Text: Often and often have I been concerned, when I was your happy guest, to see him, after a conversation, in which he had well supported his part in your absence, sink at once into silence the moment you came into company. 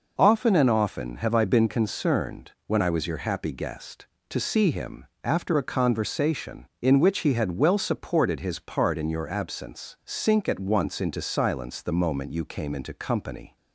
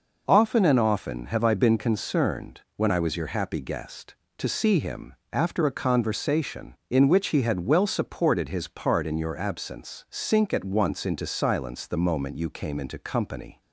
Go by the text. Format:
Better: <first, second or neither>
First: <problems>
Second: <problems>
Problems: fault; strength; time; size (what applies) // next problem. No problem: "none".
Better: neither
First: none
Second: none